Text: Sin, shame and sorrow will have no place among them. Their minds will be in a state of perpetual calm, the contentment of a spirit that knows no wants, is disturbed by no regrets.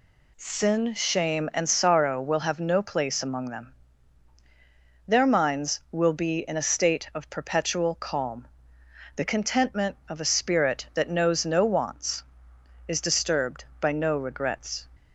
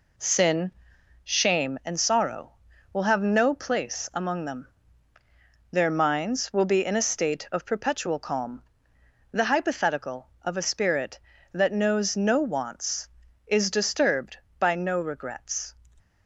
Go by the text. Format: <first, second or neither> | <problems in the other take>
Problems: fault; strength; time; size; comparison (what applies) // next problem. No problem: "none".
first | says "hypothetical" for "contentment"; at 9.4 s